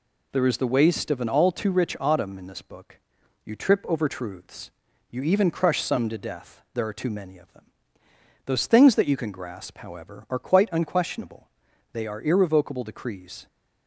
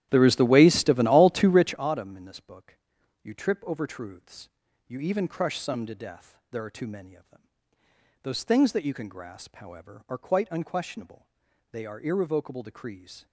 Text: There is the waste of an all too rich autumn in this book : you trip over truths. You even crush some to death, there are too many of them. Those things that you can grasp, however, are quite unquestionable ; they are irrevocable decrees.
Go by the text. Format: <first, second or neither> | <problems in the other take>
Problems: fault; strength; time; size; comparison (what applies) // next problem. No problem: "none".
first | starts louder than the rest; strong; until 1.9 s; 12 dB